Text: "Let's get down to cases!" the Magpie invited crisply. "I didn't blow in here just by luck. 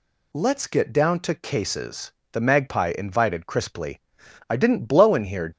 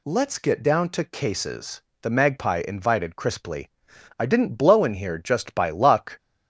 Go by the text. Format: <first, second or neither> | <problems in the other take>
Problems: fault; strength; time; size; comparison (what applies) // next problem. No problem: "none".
second | stops before "just by luck"; at 5.5 s